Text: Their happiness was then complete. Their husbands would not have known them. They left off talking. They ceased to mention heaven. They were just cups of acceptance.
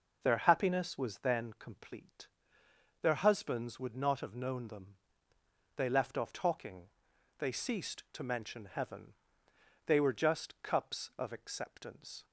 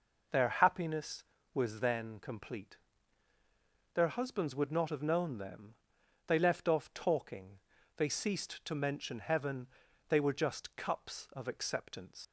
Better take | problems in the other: first | leaves "acceptance" unfinished; at 12.2 s; 80 ms

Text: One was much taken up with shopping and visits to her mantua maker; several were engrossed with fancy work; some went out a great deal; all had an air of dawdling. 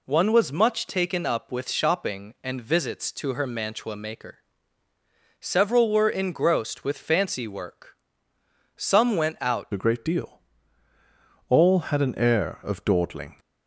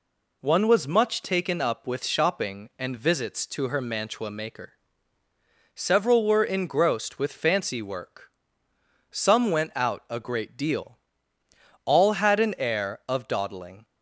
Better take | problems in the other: second | changes voice at "a"; from 9.7 s on; 3.6 s long

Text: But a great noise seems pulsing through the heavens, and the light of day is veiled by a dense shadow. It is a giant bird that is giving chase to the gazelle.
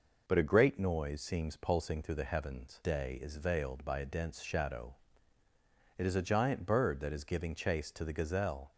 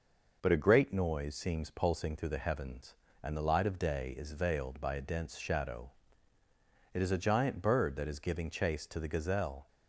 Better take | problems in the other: second | skips "and the light of"; at 2.8 s

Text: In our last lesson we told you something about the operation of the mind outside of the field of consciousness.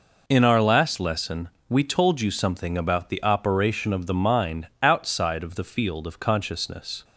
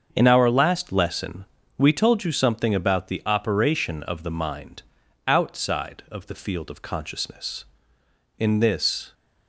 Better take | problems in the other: first | starts louder than the rest; until 1.1 s; 7 dB // pauses between "lesson" and "we"; slight; at 1.4 s; 0.32 s long; slight in the first // pauses between "mind" and "outside"; at 4.8 s; 0.42 s long; slight in the first // goes on to say "In this"; noticeable; from 8.3 s on; 0.76 s long

